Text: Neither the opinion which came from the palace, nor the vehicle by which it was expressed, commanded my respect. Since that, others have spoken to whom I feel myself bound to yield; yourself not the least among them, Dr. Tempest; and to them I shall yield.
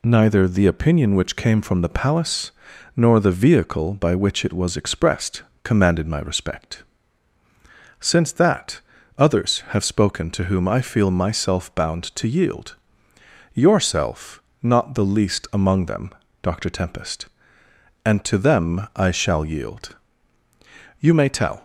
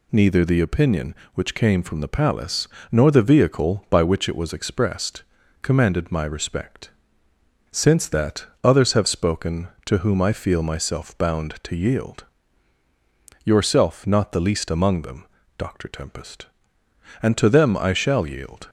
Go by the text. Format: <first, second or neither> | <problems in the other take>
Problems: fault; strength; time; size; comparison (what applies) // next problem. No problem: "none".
second | pauses between "yourself" and "not"; slight; at 14.4 s; 0.22 s long // goes on to say "You may tell"; noticeable; from 21.0 s on; 0.62 s long